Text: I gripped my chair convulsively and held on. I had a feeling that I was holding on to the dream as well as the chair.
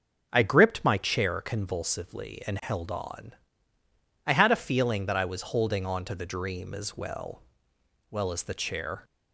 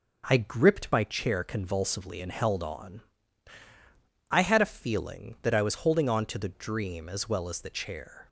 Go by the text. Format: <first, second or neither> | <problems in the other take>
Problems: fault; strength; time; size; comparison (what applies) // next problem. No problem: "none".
second | starts louder than the rest; until 1.3 s; 6.5 dB // says "well" twice; at 8.0 s